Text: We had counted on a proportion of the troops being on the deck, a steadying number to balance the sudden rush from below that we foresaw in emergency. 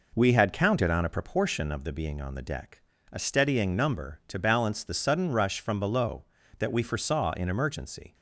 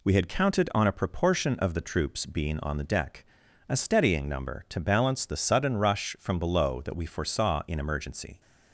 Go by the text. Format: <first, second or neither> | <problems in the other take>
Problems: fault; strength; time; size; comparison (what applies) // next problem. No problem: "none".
second | skips "troops"; at 1.9 s